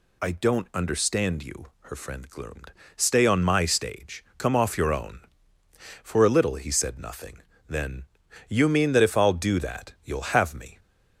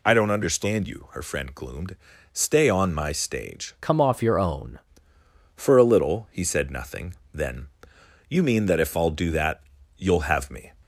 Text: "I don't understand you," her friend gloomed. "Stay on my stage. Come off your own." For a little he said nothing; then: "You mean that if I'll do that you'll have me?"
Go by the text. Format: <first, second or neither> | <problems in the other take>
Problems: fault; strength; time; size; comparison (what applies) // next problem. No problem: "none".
first | changes voice from "Come" to "own"; from 3.8 to 4.7 s; 0.9 s long // pauses between "that" and "you'll"; slight; at 9.6 s; 0.34 s long